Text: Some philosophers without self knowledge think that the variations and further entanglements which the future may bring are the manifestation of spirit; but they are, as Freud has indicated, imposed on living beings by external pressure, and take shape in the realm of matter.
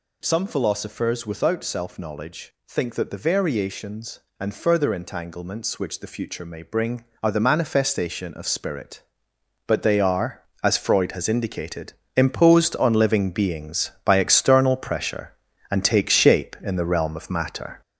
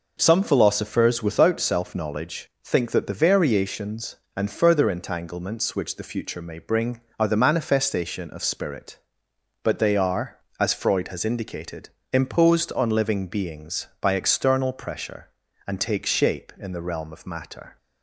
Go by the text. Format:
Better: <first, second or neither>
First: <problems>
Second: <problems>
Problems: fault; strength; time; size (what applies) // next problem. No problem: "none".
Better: second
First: gets louder; noticeable; throughout; 6 dB // pauses between "knowledge" and "think"; slight; at 2.5 s; 0.16 s long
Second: pauses between "knowledge" and "think"; slight; at 2.4 s; 0.16 s long